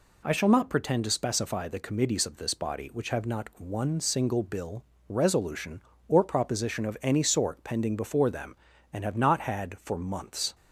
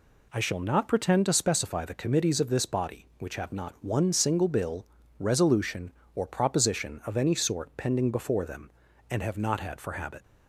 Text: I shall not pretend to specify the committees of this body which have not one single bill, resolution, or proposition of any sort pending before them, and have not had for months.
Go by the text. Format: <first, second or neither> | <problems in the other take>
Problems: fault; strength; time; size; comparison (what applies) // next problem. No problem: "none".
first | says "habit" for "months"; at 9.9 s